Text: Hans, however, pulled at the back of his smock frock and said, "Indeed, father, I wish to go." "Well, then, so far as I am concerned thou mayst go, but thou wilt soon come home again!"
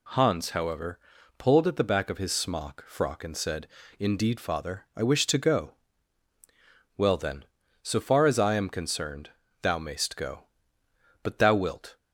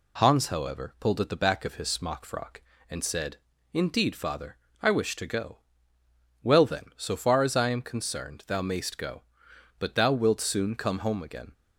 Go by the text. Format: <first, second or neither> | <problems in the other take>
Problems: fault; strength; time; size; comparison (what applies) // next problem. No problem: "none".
second | pauses between "concerned" and "thou"; slight; at 9.3 s; 0.32 s long // stops before "soon come home again"; at 11.9 s